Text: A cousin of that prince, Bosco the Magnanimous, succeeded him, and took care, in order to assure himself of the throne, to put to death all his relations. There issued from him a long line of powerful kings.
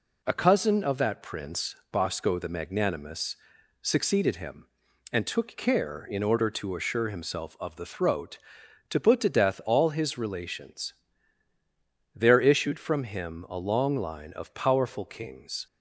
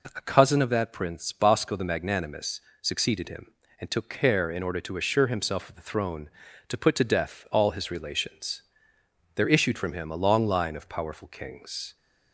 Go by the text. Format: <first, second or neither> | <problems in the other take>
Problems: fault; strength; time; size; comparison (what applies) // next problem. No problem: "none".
second | says "throat" for "throne"; at 7.8 s